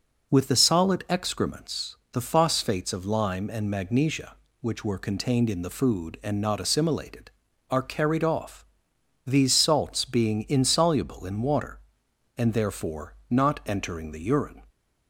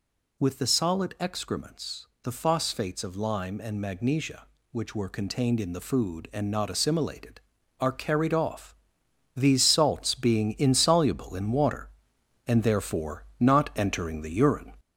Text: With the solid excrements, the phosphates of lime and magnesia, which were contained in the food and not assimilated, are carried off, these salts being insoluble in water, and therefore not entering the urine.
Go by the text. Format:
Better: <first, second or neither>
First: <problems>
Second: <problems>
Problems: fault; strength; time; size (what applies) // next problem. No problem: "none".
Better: first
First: pauses between "therefore" and "not"; slight; at 13.1 s; 0.16 s long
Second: gets louder; noticeable; throughout; 4.5 dB // pauses between "therefore" and "not"; slight; at 13.2 s; 0.16 s long